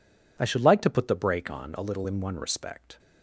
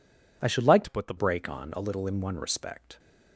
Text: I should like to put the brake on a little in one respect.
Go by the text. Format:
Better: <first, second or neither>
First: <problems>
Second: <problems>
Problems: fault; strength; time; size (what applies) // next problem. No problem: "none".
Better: first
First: none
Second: changes voice from "to" to "the"; from 0.8 to 1.1 s; 0.3 s long